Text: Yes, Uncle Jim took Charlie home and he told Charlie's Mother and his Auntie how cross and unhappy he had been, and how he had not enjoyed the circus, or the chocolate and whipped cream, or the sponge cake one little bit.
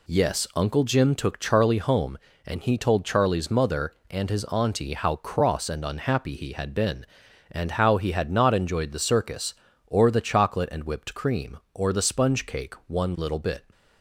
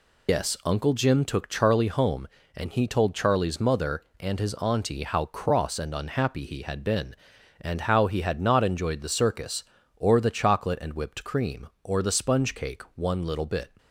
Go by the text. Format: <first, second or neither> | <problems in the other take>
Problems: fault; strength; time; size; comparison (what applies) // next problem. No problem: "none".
first | loses the start of "Yes"; at 0.2 s; 110 ms